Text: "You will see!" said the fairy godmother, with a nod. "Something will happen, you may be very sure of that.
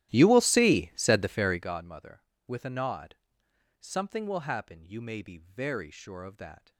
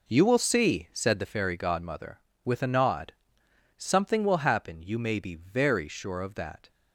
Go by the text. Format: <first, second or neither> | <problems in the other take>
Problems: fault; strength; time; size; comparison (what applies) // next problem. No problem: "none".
second | starts louder than the rest; strong; until 1.8 s; 14.5 dB